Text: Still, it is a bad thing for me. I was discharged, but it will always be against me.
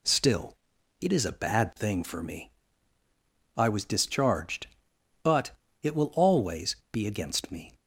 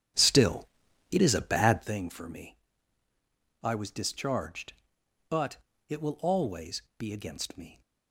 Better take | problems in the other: first | starts louder than the rest; strong; until 2.0 s; 9 dB // pauses between "but" and "it"; slight; at 5.5 s; 0.32 s long; slight in the first // pauses between "always" and "be"; slight; at 6.8 s; 0.16 s long; slight in the first

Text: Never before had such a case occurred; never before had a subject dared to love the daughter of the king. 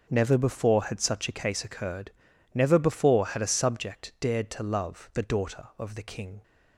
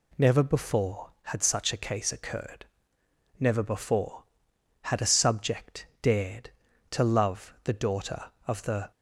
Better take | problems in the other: first | pauses between "subject" and "dared"; slight; at 5.8 s; 0.16 s long // stops before "king"; at 8.9 s

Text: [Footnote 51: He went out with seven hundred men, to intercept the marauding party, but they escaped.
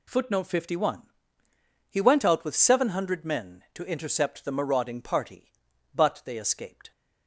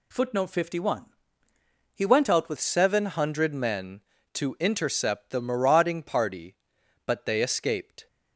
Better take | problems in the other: first | changes voice at "seven"; from 2.5 s on; 5.5 s long

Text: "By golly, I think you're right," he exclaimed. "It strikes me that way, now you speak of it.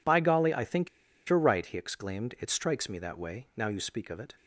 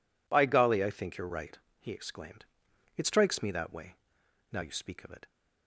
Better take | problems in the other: second | pauses between "think" and "you're"; at 0.8 s; 0.40 s long

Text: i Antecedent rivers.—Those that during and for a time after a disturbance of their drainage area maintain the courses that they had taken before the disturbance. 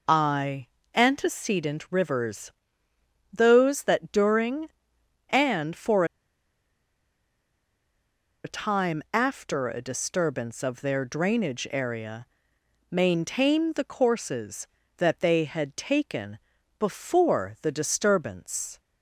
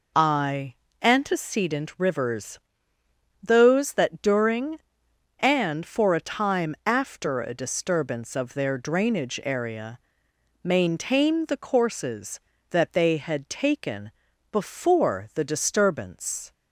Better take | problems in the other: second | pauses between "i" and "Antecedent"; slight; at 0.6 s; 0.28 s long; slight in the second // pauses between "for" and "a"; strong; at 6.0 s; 2.3 s long // pauses between "area" and "maintain"; noticeable; at 12.2 s; 0.64 s long; noticeable in the second // pauses between "taken" and "before"; at 16.3 s; 0.40 s long; also in the second

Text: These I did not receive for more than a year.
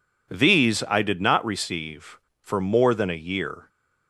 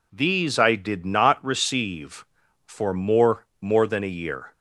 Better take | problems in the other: first | says "more" twice; at 3.6 s

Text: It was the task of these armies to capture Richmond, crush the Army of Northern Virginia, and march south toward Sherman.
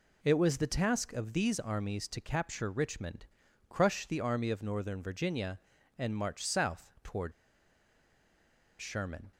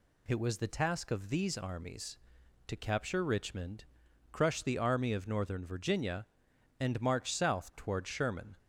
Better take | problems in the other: second | pauses between "toward" and "Sherman"; strong; at 7.3 s; 1.4 s long

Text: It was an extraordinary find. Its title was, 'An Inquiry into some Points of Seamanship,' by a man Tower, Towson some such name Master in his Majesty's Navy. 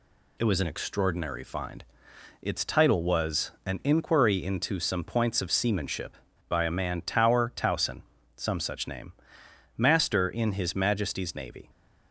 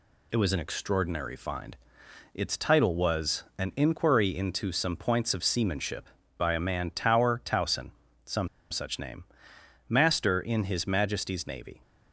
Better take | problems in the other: first | pauses between "Towson" and "some"; at 7.9 s; 0.38 s long; also in the first // pauses between "some" and "such"; slight; at 8.4 s; 0.22 s long // pauses between "name" and "Master"; noticeable; at 9.2 s; 0.62 s long; noticeable in the first

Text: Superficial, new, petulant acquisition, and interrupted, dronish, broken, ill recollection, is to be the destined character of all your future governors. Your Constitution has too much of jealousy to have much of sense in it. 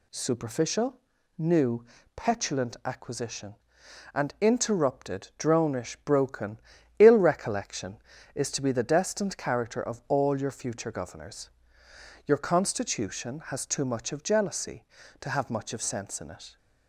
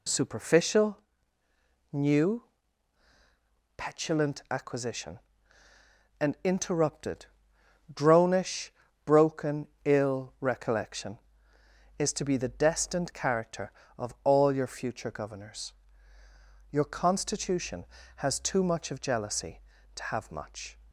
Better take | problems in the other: first | stops before "of sense in it"; at 20.8 s

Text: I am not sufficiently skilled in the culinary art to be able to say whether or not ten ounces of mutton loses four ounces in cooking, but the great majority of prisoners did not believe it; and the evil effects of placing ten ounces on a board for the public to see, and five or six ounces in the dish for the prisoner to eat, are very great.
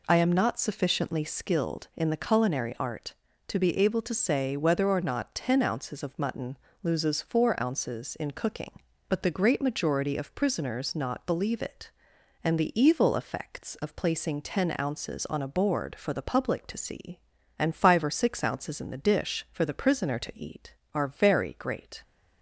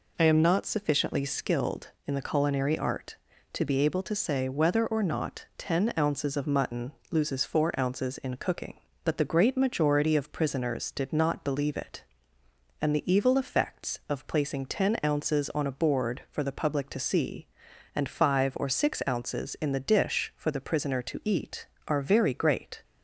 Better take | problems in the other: second | pauses between "mutton" and "loses"; slight; at 6.5 s; 0.26 s long; slight in the second // skips "did"; at 10.9 s

